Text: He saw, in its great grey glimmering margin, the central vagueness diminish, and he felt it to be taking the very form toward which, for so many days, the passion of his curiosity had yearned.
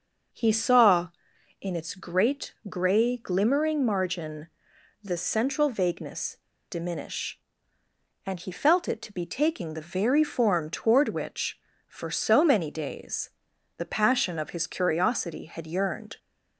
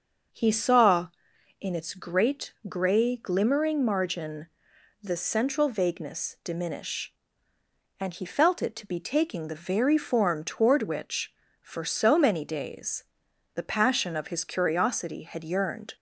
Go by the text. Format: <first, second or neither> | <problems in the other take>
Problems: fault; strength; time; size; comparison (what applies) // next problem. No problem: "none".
second | starts louder than the rest; until 1.8 s; 6 dB; also in the second // pauses between "vagueness" and "diminish"; slight; at 6.3 s; 0.33 s long